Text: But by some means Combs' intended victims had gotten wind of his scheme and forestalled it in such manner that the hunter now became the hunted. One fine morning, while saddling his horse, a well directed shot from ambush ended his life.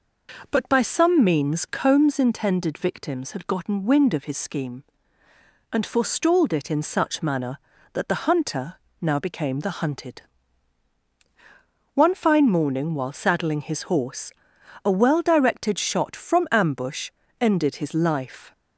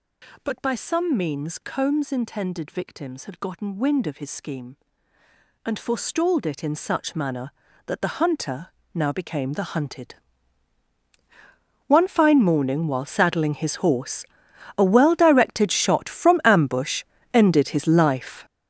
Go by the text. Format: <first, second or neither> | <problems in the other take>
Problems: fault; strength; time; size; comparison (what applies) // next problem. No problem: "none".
first | gets louder; strong; throughout; 12 dB // pauses between "hunter" and "now"; slight; at 8.6 s; 0.26 s long; slight in the first // pauses between "ambush" and "ended"; slight; at 17.0 s; 0.30 s long; slight in the first